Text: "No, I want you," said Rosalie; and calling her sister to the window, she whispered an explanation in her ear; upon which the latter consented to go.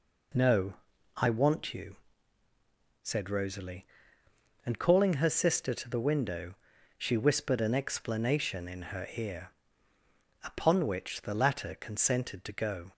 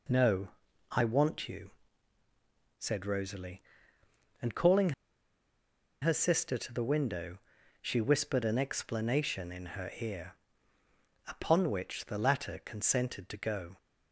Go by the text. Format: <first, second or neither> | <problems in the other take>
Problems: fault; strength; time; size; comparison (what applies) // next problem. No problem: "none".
first | pauses between "calling" and "her"; at 4.9 s; 1.1 s long